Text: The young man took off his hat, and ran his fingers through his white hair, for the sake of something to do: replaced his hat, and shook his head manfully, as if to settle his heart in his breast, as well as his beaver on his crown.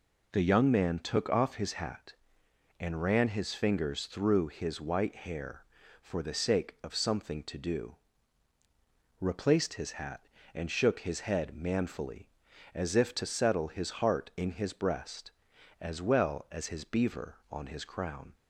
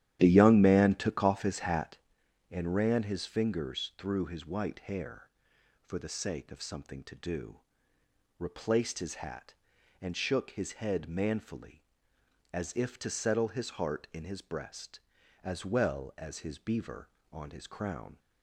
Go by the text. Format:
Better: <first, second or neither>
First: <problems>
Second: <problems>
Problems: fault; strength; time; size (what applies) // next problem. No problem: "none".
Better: first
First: none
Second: starts louder than the rest; strong; until 2.0 s; 11.5 dB